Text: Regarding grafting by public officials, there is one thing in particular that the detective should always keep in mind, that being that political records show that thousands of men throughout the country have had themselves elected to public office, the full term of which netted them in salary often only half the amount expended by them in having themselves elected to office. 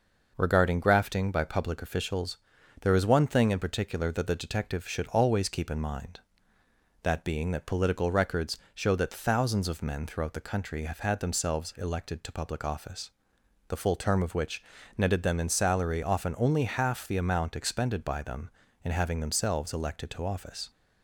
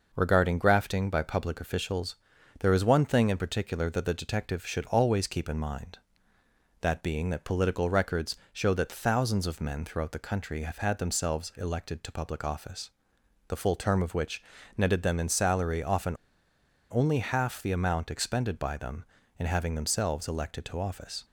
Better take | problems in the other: first | pauses between "records" and "show"; slight; at 8.3 s; 0.18 s long; slight in the first // pauses between "which" and "netted"; slight; at 14.4 s; 0.34 s long; slight in the first // pauses between "often" and "only"; noticeable; at 16.1 s; 0.77 s long

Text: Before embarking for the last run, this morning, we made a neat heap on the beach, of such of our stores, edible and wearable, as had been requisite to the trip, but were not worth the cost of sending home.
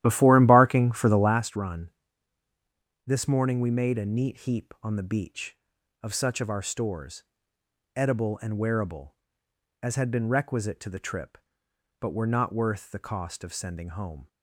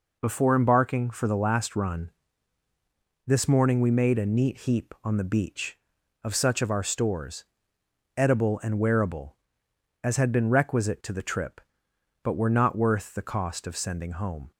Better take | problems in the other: second | starts louder than the rest; strong; until 1.4 s; 13 dB

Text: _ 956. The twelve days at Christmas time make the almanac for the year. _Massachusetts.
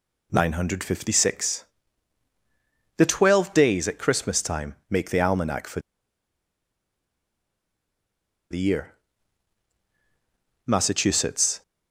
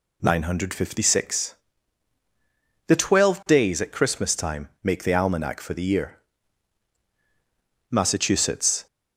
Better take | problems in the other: second | pauses between "for" and "the"; strong; at 5.8 s; 2.6 s long

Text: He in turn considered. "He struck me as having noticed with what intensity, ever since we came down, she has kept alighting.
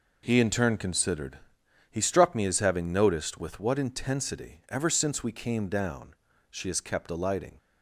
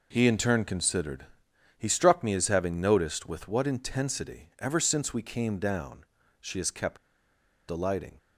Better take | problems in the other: first | pauses between "kept" and "alighting"; noticeable; at 6.9 s; 0.71 s long

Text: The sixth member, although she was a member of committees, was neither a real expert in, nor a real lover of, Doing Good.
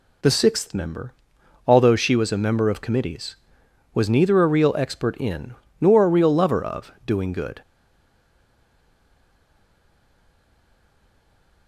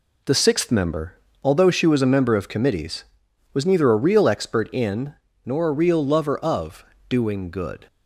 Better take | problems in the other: second | stays silent after the last word; strong; from 7.6 s on; 4.0 s long

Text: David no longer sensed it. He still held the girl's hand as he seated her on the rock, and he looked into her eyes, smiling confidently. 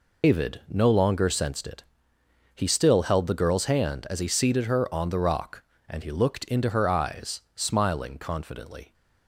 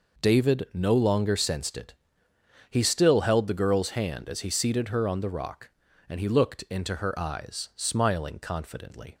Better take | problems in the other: second | loses the start of "David"; at 0.2 s; 105 ms

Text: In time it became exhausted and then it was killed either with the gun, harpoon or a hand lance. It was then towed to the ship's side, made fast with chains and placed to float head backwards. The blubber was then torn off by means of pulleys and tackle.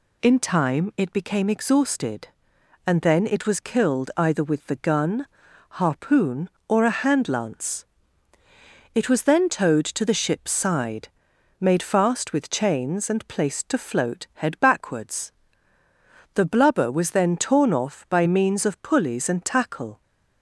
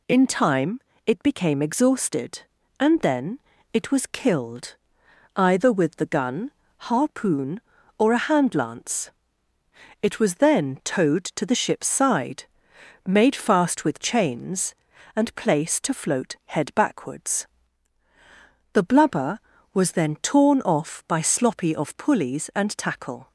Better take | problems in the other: first | pauses between "time" and "it"; slight; at 0.7 s; 0.26 s long // pauses between "then" and "it"; slight; at 3.3 s; 0.34 s long // pauses between "killed" and "either"; noticeable; at 4.7 s; 0.58 s long // says "sloppy" for "means"; at 21.2 s

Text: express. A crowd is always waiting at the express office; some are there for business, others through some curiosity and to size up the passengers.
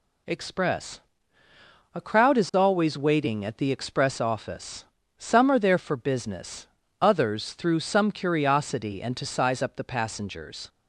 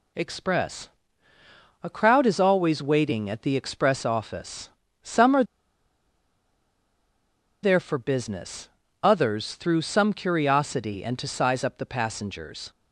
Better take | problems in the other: first | pauses between "are" and "there"; strong; at 5.4 s; 2.1 s long

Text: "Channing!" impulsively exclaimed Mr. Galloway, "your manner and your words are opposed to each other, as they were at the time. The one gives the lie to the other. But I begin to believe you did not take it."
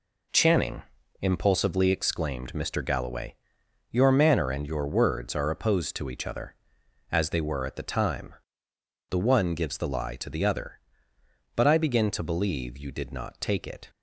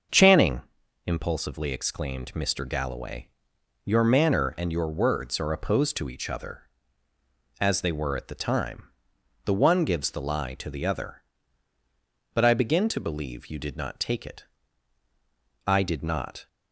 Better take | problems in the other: first | starts louder than the rest; until 1.5 s; 6 dB // goes on to say "I did not"; noticeable; from 15.6 s on; 0.80 s long

